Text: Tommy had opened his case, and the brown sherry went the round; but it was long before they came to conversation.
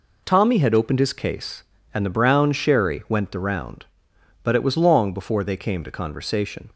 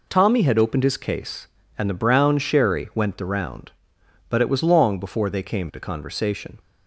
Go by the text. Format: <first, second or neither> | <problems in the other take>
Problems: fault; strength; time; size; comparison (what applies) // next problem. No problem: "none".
neither | none